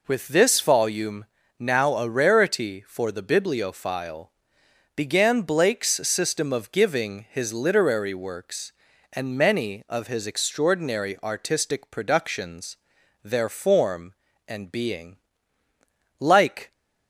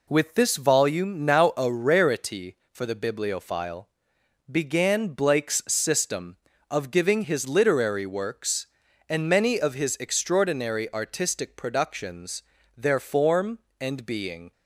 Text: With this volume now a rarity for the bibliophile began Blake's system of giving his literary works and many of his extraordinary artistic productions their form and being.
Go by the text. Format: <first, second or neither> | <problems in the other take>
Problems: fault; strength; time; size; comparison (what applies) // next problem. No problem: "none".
second | pauses between "volume" and "now"; slight; at 1.2 s; 0.34 s long // pauses between "bibliophile" and "began"; noticeable; at 4.3 s; 0.65 s long; noticeable in the second // pauses between "productions" and "their"; noticeable; at 12.7 s; 0.48 s long; slight in the second // goes on to say "Like"; from 16.1 s on; 0.54 s long